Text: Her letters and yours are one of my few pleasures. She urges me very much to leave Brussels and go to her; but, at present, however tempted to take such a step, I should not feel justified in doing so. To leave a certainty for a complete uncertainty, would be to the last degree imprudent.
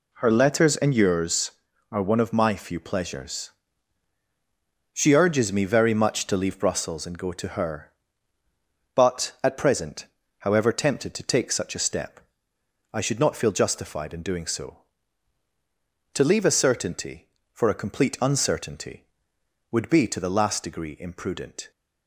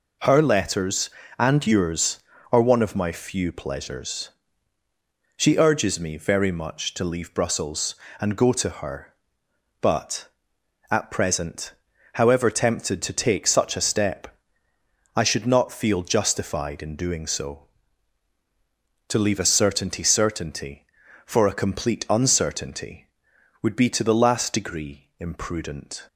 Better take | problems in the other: first | says "certainty" twice; at 20.0 s

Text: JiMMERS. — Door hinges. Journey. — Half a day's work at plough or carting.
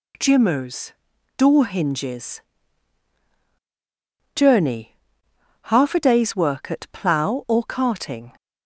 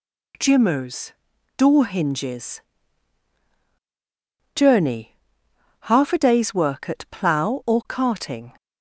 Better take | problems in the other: neither | none

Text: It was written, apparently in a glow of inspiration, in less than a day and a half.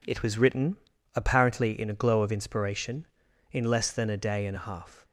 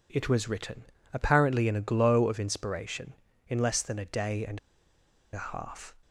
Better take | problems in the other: first | pauses between "and" and "a"; noticeable; at 4.5 s; 0.74 s long

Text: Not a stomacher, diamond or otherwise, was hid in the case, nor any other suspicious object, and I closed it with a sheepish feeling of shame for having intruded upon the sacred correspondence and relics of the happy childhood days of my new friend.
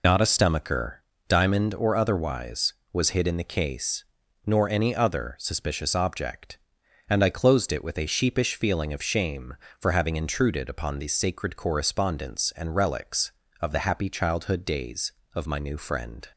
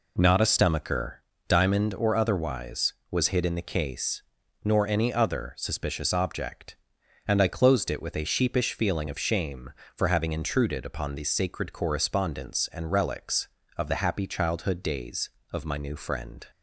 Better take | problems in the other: second | loses the start of "Not"; at 0.0 s; 85 ms

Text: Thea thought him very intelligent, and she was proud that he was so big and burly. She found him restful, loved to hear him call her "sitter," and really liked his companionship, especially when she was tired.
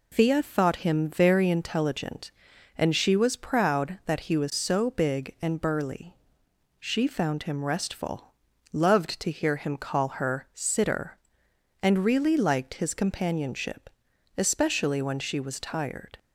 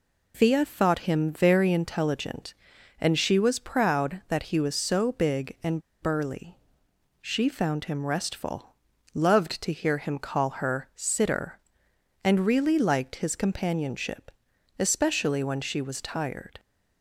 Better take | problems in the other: first | pauses between "and" and "burly"; slight; at 5.8 s; 0.20 s long

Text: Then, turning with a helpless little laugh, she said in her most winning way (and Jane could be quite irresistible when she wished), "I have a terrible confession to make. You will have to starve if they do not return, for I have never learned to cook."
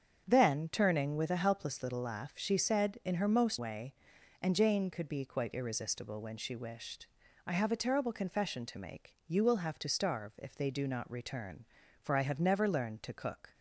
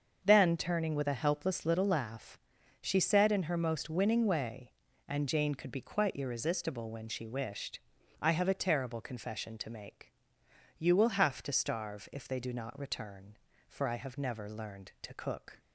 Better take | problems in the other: second | starts louder than the rest; strong; until 1.2 s; 7.5 dB; also in the second // skips "winning"; at 3.5 s

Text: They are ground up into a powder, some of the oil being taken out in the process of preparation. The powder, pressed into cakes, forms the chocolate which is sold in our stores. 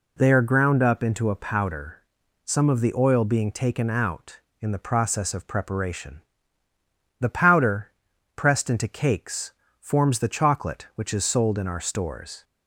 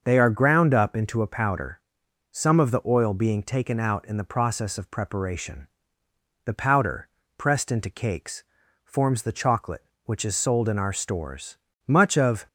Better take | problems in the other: first | starts louder than the rest; until 1.0 s; 6.5 dB // goes on to say "Much of"; from 11.8 s on; 0.60 s long

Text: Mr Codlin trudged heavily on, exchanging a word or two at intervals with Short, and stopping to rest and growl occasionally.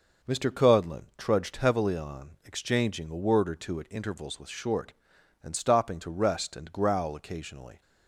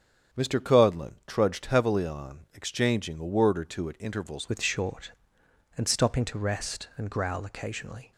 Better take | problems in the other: first | starts louder than the rest; strong; until 1.4 s; 8 dB // changes voice at "with"; from 4.4 s on; 3.7 s long

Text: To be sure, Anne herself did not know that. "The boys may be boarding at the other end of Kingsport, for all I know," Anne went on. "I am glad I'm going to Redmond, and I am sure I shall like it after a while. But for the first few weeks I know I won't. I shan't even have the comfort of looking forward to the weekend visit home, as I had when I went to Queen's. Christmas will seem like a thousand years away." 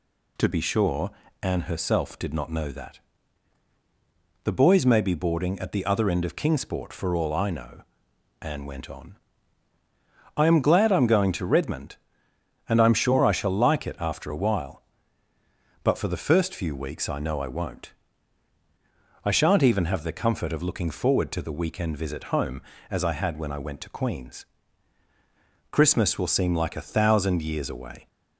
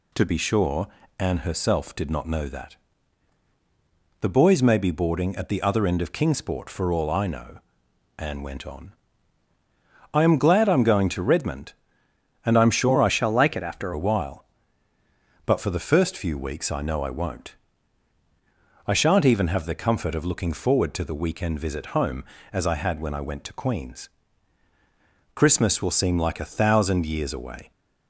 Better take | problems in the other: first | changes voice from "shall" to "after"; from 13.0 to 13.9 s; 0.9 s long

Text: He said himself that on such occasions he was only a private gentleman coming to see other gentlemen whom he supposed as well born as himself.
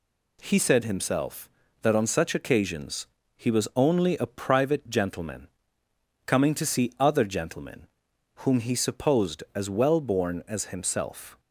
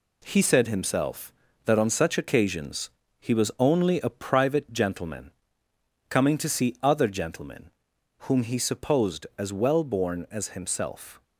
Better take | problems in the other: first | gets quieter; noticeable; throughout; 6 dB // pauses between "occasions" and "he"; slight; at 2.8 s; 0.30 s long; slight in the first // pauses between "gentleman" and "coming"; noticeable; at 5.3 s; 0.78 s long; noticeable in the first // pauses between "gentlemen" and "whom"; noticeable; at 7.7 s; 0.56 s long; noticeable in the first

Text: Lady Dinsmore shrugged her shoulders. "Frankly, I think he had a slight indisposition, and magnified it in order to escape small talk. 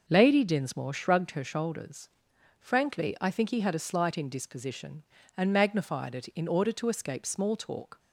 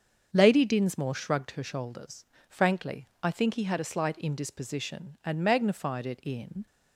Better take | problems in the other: first | starts louder than the rest; until 1.3 s; 7 dB // stops before "order to escape small talk"; at 6.6 s

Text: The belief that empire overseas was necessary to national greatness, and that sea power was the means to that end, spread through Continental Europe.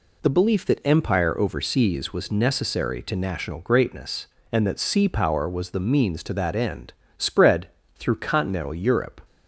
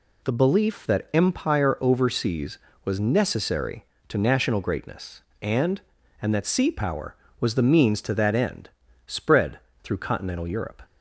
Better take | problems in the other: first | says "and" twice; at 6.2 s // pauses between "spread" and "through"; slight; at 9.5 s; 0.24 s long; slight in the first

